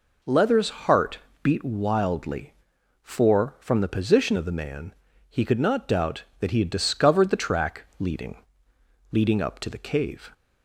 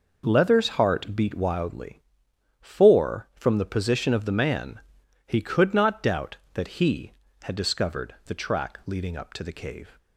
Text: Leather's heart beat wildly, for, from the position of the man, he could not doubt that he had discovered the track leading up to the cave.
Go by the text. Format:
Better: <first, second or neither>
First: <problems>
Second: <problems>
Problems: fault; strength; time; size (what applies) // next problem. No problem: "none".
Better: second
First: pauses between "heart" and "beat"; slight; at 1.1 s; 0.24 s long // says "leading" twice; at 9.1 s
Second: none